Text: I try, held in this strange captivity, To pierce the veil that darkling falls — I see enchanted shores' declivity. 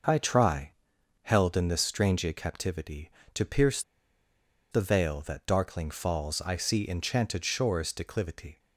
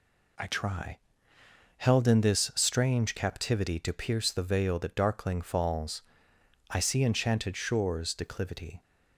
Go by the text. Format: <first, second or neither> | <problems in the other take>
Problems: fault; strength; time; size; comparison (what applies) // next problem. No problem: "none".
second | pauses between "pierce" and "the"; noticeable; at 3.8 s; 0.90 s long